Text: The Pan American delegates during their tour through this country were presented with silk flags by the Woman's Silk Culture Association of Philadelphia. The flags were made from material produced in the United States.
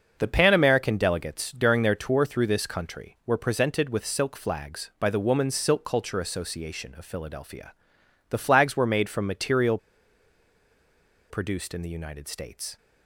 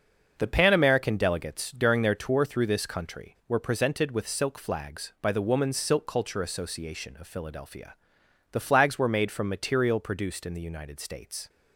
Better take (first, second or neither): second